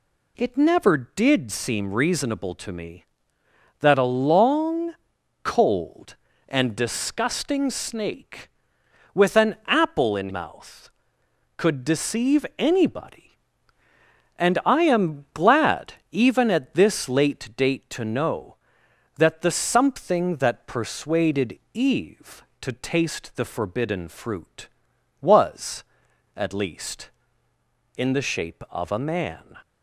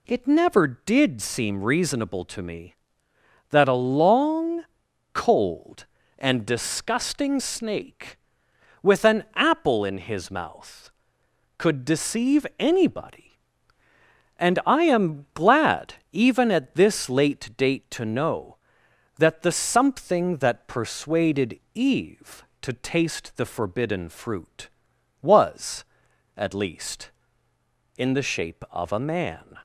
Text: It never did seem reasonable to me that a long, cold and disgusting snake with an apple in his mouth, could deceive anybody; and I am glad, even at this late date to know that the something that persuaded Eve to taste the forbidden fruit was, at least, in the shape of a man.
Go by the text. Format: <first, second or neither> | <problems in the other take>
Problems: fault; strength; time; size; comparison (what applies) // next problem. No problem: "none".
second | skips "his"; at 10.2 s // pauses between "persuaded" and "Eve"; slight; at 21.5 s; 0.16 s long; slight in the second